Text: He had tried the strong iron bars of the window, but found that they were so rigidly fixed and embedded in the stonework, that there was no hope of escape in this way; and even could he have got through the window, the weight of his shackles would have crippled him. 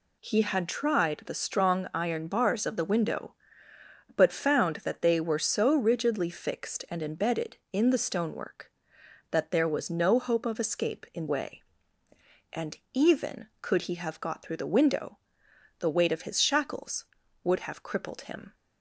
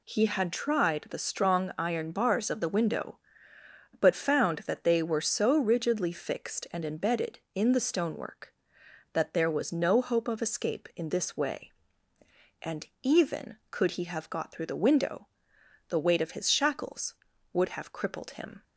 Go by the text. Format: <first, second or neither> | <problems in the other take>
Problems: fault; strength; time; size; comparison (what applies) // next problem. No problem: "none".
second | skips "this"; at 11.2 s // pauses between "and" and "even"; slight; at 12.7 s; 0.16 s long; slight in the second